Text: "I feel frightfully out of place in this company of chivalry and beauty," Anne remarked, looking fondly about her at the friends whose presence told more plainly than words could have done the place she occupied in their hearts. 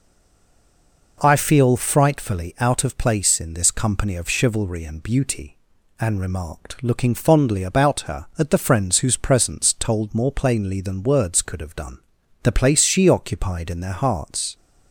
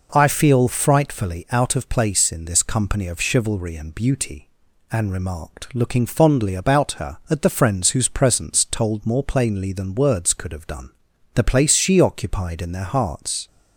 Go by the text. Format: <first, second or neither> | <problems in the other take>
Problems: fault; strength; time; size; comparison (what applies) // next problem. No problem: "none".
second | stays silent before the first word; until 1.1 s; 1.1 s long // pauses between "done" and "the"; at 11.9 s; 0.44 s long; also in the second